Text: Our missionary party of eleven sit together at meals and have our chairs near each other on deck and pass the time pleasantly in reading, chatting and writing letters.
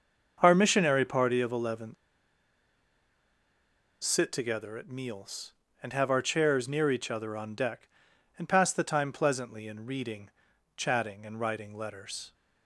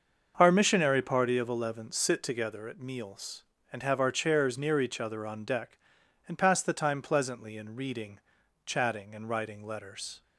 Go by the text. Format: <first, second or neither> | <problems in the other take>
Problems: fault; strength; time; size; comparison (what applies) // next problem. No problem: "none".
second | starts louder than the rest; until 1.4 s; 6.5 dB; also in the second // pauses between "eleven" and "sit"; strong; at 1.9 s; 2.0 s long